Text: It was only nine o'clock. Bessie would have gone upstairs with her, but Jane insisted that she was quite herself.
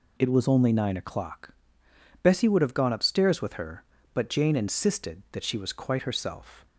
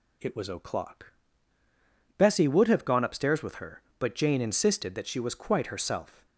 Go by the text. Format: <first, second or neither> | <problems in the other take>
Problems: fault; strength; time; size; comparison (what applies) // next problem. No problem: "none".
first | skips "only nine"; at 0.4 s